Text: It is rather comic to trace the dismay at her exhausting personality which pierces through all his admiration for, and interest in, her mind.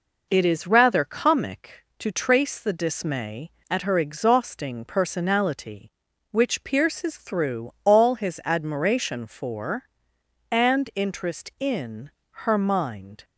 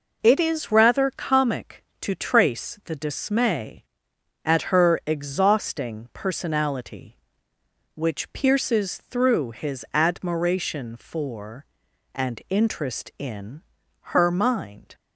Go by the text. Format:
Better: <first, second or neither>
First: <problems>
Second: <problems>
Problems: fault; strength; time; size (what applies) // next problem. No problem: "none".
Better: first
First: none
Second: skips "all"; at 9.5 s